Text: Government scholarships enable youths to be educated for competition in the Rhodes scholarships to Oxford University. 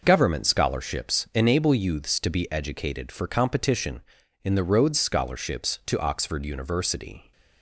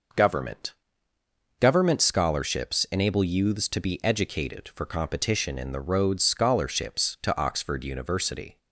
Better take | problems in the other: first | says "Government" twice; at 1.5 s

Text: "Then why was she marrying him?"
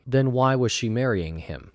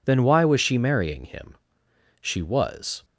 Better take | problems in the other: first | goes on to say "She was"; noticeable; from 2.2 s on; 0.84 s long

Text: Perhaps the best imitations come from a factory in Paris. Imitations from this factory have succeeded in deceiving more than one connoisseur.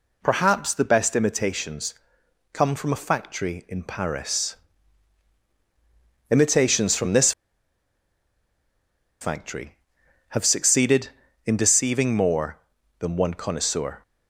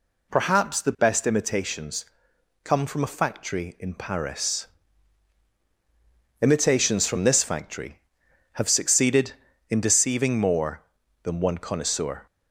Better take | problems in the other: second | pauses between "imitations" and "come"; noticeable; at 1.9 s; 0.56 s long; noticeable in the second // pauses between "this" and "factory"; strong; at 7.3 s; 1.9 s long

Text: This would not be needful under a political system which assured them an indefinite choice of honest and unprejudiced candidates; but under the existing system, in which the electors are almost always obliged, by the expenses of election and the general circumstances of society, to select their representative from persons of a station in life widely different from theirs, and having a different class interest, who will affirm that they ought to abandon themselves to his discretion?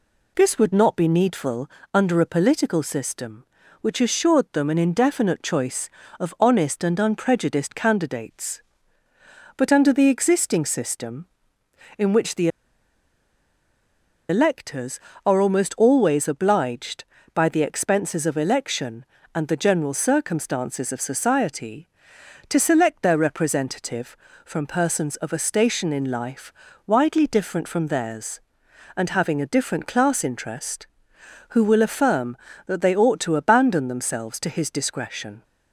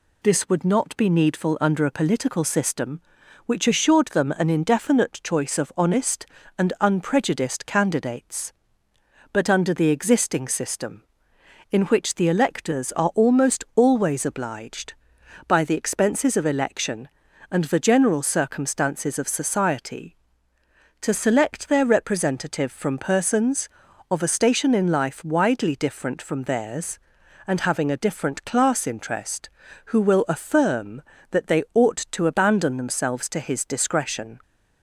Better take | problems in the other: second | pauses between "needful" and "under"; slight; at 1.6 s; 0.24 s long // pauses between "the" and "electors"; strong; at 12.4 s; 1.8 s long // pauses between "life" and "widely"; slight; at 26.5 s; 0.36 s long

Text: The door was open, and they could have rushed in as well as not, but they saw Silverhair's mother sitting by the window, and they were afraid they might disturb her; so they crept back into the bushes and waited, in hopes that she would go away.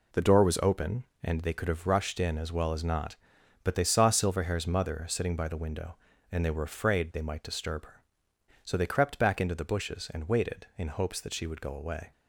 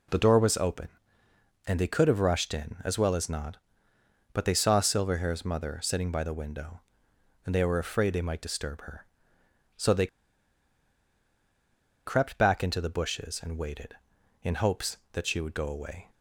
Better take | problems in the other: first | pauses between "they" and "crept"; strong; at 10.0 s; 1.9 s long

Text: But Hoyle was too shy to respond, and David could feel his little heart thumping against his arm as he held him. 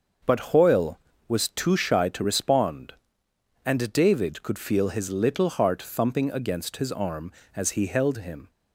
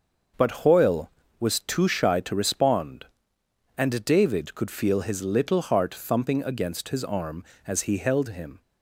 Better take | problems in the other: neither | starts louder than the rest; the same in both

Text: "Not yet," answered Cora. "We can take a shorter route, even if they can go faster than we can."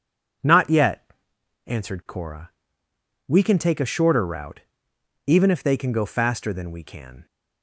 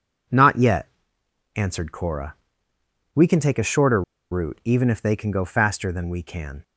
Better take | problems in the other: first | pauses between "shorter" and "route"; slight; at 4.0 s; 0.29 s long

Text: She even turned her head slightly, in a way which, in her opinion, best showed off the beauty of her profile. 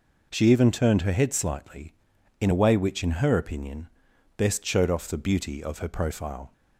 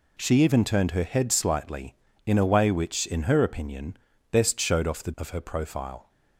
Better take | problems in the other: first | skips "beauty"; at 5.1 s

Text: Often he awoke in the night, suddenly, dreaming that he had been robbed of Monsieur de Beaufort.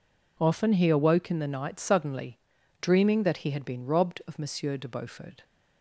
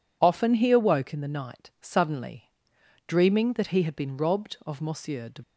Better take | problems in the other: first | stops before "Beaufort"; at 5.4 s

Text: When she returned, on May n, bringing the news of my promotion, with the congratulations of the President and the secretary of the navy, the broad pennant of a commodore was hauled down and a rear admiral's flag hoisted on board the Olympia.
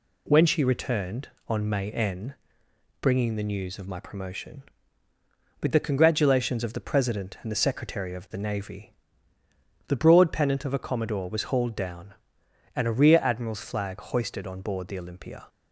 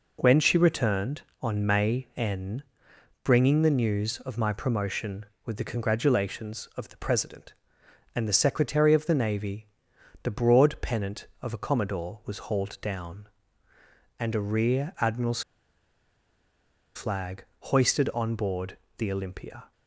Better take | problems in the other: first | pauses between "admiral's" and "flag"; strong; at 15.4 s; 1.5 s long // pauses between "board" and "the"; slight; at 18.7 s; 0.22 s long

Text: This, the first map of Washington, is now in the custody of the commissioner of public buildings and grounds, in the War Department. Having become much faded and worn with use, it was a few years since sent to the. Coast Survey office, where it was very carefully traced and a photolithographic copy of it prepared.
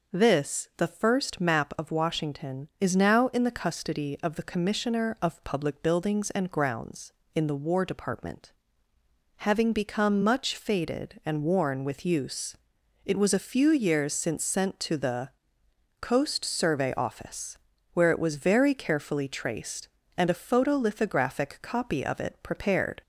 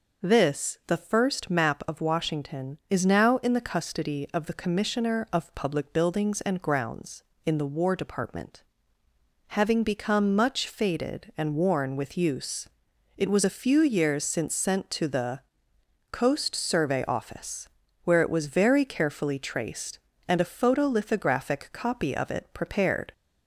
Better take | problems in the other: neither | none

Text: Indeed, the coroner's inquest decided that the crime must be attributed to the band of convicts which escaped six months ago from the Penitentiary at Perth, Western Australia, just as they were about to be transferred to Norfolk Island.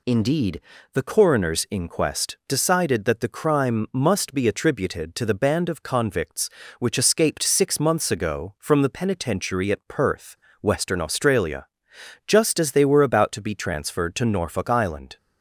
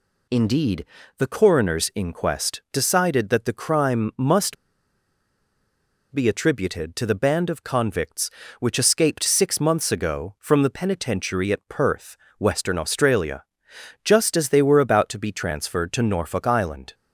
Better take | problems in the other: first | pauses between "must" and "be"; strong; at 4.5 s; 1.5 s long

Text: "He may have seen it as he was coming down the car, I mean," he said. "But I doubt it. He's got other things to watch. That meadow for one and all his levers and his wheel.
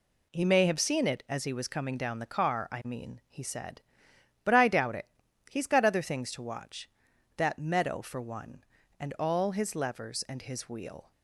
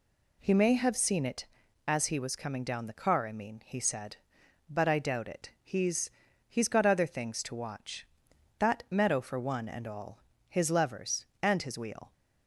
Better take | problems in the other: first | says "He's" twice; at 6.4 s // pauses between "all" and "his"; slight; at 10.1 s; 0.28 s long

